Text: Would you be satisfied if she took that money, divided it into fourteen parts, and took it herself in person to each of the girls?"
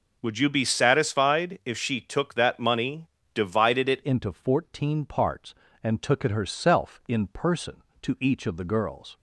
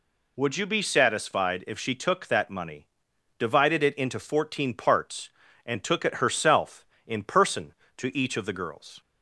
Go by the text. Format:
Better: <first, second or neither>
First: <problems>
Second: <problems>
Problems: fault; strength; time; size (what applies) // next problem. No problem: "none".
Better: second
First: changes voice at "into"; from 4.0 s on; 5.1 s long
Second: none